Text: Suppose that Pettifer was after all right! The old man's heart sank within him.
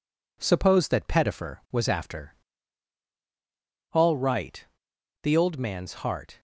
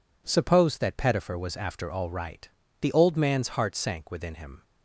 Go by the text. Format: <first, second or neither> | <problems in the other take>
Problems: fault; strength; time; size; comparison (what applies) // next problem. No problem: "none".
second | pauses between "after" and "all"; strong; at 2.3 s; 1.6 s long // stops before "sank within him"; at 6.3 s